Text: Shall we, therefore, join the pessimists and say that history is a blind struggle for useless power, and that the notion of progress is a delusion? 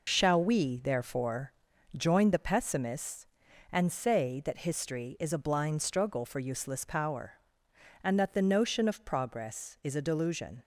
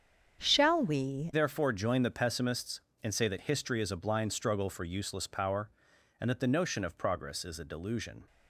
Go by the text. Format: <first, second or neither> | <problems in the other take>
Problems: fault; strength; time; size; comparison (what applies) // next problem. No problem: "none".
first | starts louder than the rest; strong; until 1.4 s; 8 dB // changes voice at "therefore"; from 1.3 s on; 6.9 s long